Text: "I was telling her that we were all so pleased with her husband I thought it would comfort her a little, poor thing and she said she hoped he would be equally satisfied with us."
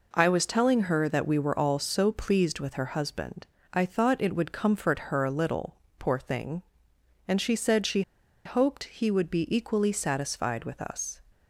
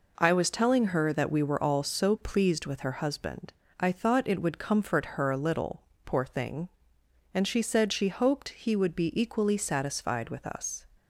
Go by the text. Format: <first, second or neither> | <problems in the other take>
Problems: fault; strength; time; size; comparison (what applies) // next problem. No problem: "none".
second | pauses between "husband" and "I"; slight; at 3.4 s; 0.26 s long; slight in the second // pauses between "she" and "hoped"; at 8.0 s; 0.44 s long